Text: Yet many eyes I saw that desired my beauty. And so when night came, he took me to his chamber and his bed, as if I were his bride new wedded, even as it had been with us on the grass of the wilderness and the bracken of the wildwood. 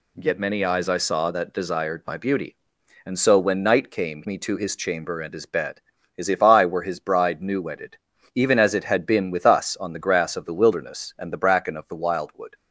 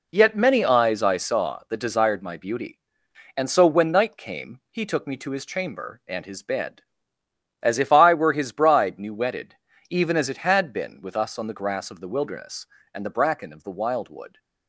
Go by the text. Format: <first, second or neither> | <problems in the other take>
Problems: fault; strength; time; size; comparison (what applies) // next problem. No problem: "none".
second | skips "he took"; at 4.2 s